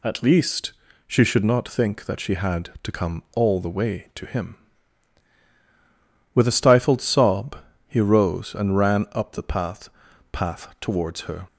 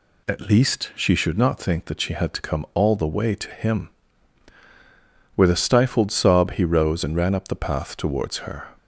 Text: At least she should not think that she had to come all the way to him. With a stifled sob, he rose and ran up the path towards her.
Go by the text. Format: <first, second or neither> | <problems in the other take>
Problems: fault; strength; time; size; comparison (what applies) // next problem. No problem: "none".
second | pauses between "least" and "she"; slight; at 0.7 s; 0.34 s long // says "path" twice; at 10.3 s